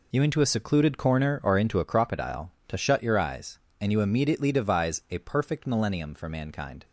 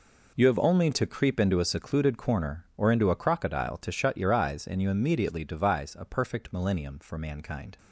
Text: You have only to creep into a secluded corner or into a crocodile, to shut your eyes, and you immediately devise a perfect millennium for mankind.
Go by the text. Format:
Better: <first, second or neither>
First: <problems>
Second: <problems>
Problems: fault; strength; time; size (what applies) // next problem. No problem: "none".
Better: second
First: skips "have only to creep"; at 0.2 s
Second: none